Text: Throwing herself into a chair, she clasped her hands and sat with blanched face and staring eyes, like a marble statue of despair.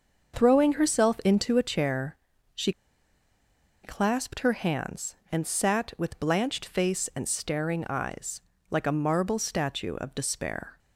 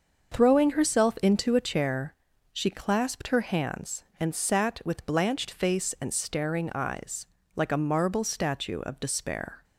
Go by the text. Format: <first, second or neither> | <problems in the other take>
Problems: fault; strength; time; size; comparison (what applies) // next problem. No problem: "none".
second | starts louder than the rest; until 1.3 s; 6.5 dB; also in the second // pauses between "she" and "clasped"; at 2.7 s; 1.1 s long